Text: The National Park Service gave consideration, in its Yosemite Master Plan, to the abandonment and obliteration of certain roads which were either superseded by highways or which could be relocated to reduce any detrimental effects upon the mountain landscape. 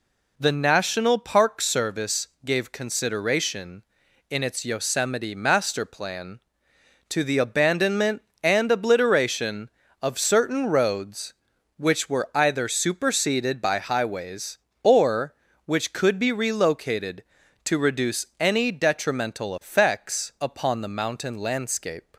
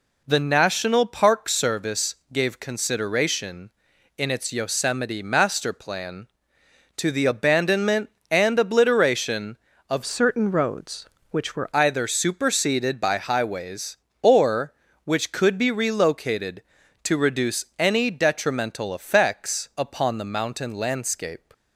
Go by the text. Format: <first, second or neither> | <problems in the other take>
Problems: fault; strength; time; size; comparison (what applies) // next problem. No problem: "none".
first | pauses between "Service" and "gave"; slight; at 2.1 s; 0.16 s long; slight in the first // changes voice from "certain" to "were"; from 10.0 to 11.6 s; 1.6 s long